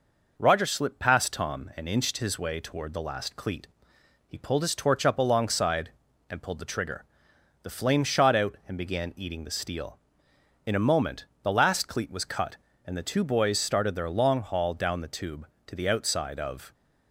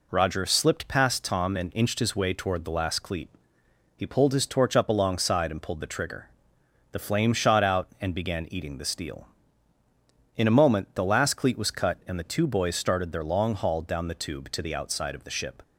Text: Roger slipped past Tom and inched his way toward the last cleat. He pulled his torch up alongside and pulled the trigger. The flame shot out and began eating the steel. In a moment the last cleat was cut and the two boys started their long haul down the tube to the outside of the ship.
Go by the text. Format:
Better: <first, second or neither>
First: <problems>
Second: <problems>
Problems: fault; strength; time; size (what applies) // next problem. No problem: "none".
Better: second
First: pauses between "moment" and "the"; slight; at 11.2 s; 0.18 s long // stops before "the ship"; at 16.7 s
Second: none